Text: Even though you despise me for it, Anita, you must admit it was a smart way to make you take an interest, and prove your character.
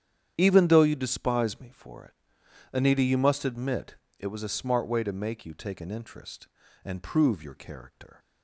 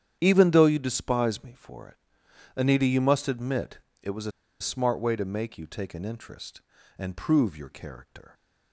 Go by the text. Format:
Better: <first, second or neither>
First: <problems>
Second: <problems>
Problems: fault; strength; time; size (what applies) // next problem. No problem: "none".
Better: first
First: starts louder than the rest; strong; until 1.3 s; 9.5 dB // pauses between "admit" and "it"; slight; at 3.9 s; 0.22 s long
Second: starts louder than the rest; strong; until 1.2 s; 9.5 dB // pauses between "admit" and "it"; slight; at 3.8 s; 0.22 s long // pauses between "a" and "smart"; slight; at 4.3 s; 0.30 s long